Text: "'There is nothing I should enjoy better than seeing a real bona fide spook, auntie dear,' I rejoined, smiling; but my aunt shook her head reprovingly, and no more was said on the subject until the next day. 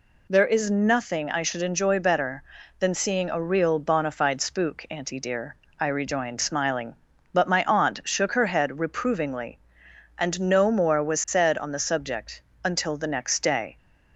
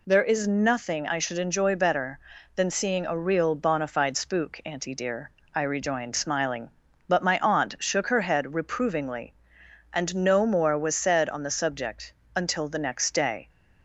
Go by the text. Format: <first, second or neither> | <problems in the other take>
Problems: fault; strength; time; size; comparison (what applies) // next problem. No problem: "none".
neither | pauses between "subject" and "until"; slight; the same in both